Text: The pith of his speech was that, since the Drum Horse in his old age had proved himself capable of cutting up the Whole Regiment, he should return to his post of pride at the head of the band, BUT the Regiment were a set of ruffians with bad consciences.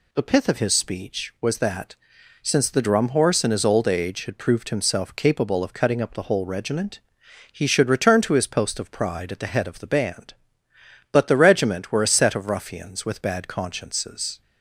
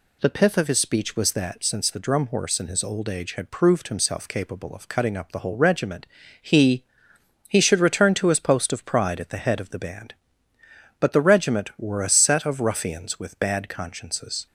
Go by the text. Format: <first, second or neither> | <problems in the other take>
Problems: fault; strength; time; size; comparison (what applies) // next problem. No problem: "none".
first | says "he" twice; at 7.4 s